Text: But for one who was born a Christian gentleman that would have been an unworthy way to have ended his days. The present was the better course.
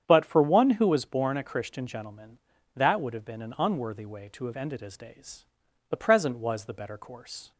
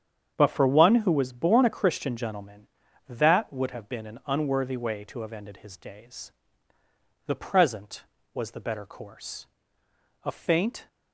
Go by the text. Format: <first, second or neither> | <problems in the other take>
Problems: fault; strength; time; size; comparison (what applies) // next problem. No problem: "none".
first | starts louder than the rest; strong; until 1.3 s; 8 dB; strong in the first // goes on to say "A faint"; noticeable; from 10.2 s on; 0.64 s long